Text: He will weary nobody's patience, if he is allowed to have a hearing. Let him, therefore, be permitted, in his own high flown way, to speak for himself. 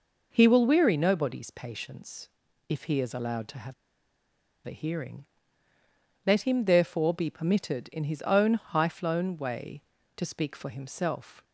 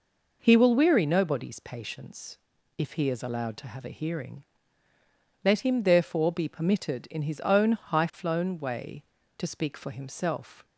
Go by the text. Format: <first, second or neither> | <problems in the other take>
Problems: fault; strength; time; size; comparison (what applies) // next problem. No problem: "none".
second | pauses between "have" and "a"; noticeable; at 3.7 s; 0.91 s long